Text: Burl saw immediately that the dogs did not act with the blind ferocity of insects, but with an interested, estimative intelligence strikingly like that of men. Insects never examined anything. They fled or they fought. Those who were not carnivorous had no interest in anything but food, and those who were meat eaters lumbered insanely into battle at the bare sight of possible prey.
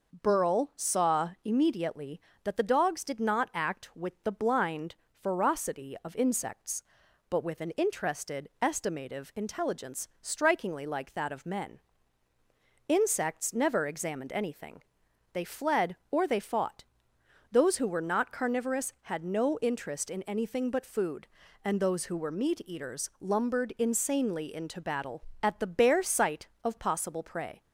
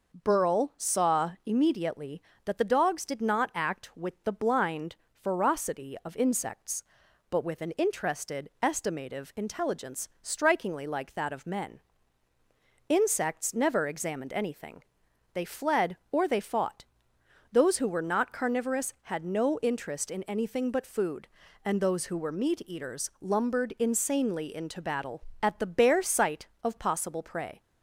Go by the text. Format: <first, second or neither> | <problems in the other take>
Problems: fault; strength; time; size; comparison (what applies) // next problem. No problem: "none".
neither | pauses between "blind" and "ferocity"; slight; the same in both